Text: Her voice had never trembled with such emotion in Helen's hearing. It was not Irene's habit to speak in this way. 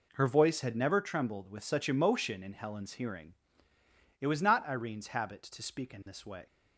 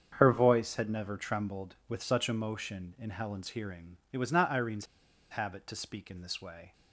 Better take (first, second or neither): first